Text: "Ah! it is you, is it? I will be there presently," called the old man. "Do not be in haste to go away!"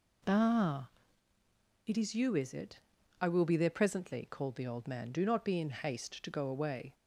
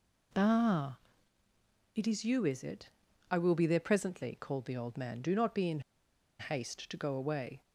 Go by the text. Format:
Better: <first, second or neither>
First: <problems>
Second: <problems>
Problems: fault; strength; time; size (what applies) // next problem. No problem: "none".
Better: first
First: none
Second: pauses between "in" and "haste"; noticeable; at 5.8 s; 0.59 s long